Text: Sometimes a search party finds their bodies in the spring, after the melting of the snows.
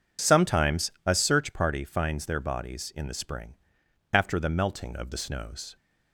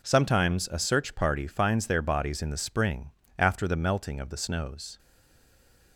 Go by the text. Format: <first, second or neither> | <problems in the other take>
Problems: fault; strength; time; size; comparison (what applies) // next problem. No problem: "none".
first | stays silent after the last word; from 4.9 s on; 1.0 s long